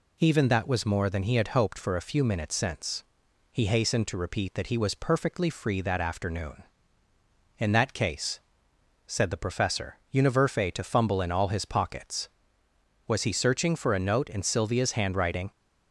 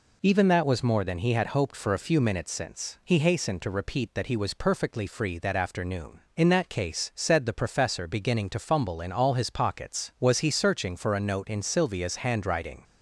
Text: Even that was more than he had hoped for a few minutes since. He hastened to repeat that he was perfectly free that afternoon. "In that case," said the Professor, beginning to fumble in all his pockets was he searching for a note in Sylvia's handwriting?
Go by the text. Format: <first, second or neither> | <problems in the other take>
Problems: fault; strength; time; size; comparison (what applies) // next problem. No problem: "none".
second | says "univerfe" for "beginning"; at 10.1 s